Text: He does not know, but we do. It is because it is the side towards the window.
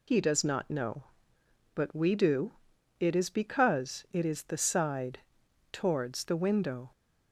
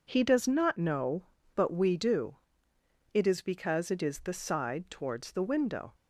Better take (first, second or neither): second